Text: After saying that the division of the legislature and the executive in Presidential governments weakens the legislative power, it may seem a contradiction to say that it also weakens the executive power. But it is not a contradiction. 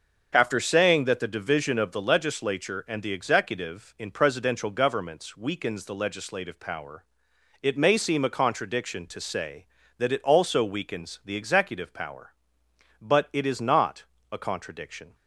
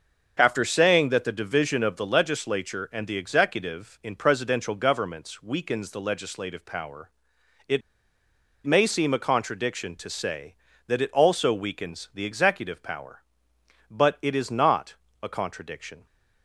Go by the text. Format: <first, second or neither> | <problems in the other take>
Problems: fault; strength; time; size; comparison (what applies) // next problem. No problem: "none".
first | starts louder than the rest; until 1.3 s; 6.5 dB; also in the first // pauses between "it" and "may"; noticeable; at 7.8 s; 0.84 s long // pauses between "not" and "a"; slight; at 14.9 s; 0.26 s long; slight in the first